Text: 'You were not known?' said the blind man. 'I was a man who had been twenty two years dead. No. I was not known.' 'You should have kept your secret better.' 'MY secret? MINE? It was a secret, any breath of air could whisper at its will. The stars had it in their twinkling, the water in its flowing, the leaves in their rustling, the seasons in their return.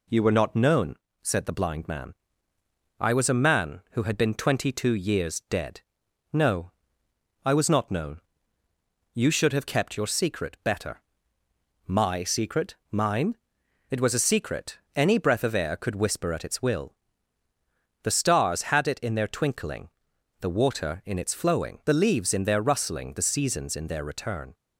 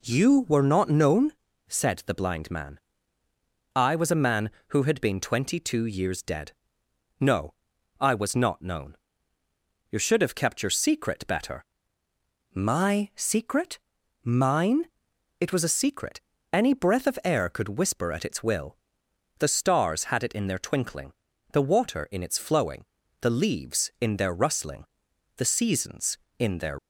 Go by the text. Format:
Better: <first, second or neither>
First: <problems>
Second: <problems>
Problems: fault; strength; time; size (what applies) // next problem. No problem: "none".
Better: first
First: none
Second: stops before "return"; at 26.7 s